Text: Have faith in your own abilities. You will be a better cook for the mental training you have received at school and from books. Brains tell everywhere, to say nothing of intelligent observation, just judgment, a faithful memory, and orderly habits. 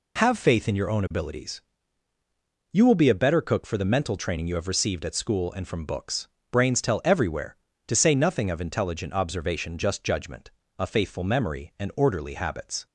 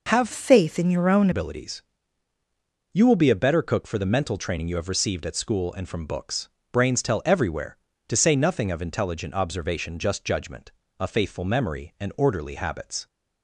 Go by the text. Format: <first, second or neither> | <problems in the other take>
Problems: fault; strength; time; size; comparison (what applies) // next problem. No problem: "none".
first | changes voice from "faith" to "own"; from 0.3 to 1.2 s; 0.9 s long